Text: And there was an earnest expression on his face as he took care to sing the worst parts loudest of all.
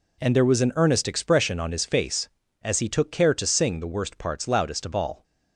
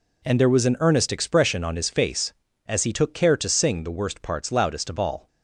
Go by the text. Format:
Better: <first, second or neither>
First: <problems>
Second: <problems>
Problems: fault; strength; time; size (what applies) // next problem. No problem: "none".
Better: neither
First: none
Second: none